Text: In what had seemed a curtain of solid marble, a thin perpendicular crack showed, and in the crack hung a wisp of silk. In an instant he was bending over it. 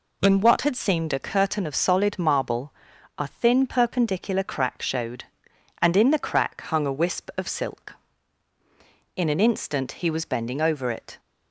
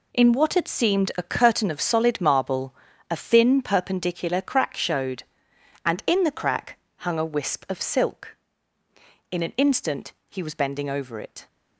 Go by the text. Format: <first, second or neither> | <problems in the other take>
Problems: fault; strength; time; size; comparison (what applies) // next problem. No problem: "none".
first | gets quieter; strong; throughout; 11.5 dB // pauses between "crack" and "hung"; slight; at 6.7 s; 0.20 s long